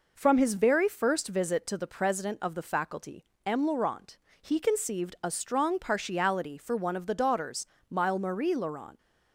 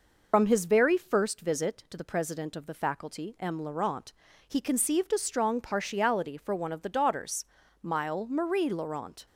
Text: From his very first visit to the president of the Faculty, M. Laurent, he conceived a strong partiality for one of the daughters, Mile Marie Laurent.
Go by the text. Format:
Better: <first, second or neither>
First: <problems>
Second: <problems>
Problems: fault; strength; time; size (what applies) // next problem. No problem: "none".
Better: first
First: none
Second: loses the start of "From"; at 0.3 s; 60 ms